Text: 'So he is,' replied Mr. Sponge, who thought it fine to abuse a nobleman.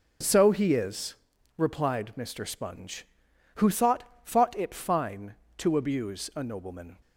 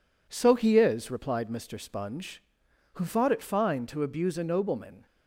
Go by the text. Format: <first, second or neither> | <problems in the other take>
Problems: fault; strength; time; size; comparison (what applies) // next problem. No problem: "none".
second | says "thought" twice; at 4.2 s